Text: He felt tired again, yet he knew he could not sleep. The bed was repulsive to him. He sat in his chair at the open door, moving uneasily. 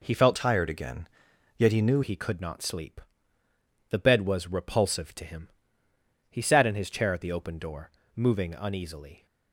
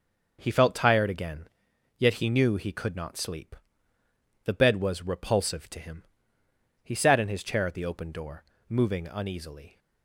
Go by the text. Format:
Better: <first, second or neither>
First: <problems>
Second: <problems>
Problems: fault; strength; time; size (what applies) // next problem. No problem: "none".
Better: second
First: changes voice from "tired" to "knew"; from 0.3 to 2.0 s; 1.7 s long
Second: none